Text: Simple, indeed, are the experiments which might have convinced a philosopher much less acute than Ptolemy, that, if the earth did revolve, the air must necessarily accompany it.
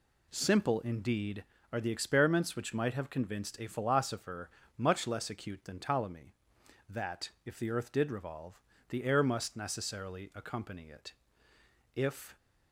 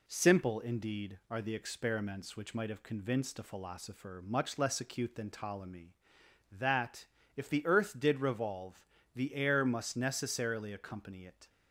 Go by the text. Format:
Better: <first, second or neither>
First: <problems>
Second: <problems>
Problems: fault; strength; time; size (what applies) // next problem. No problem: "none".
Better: second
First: pauses between "philosopher" and "much"; slight; at 4.5 s; 0.26 s long // goes on to say "If"; slight; from 11.9 s on; 0.42 s long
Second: none